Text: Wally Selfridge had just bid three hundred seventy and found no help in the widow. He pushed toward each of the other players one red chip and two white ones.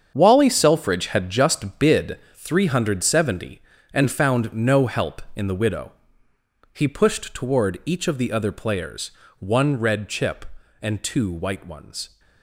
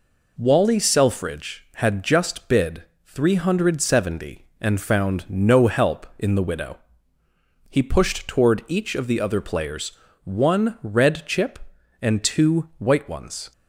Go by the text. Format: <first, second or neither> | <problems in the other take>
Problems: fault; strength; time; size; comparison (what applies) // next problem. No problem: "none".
second | gets quieter; strong; throughout; 11 dB // pauses between "bid" and "three"; slight; at 2.1 s; 0.16 s long; slight in the second // pauses between "players" and "one"; slight; at 9.0 s; 0.30 s long; slight in the second